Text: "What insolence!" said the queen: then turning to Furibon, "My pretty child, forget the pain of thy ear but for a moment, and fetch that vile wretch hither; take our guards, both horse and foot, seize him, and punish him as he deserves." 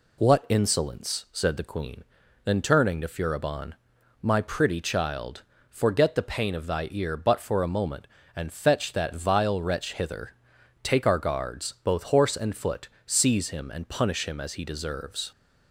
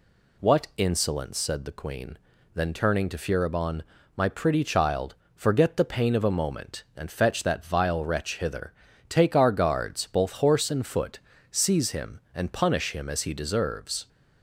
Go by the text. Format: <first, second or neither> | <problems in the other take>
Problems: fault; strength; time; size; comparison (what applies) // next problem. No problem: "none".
first | skips "thy ear but for"; at 6.2 s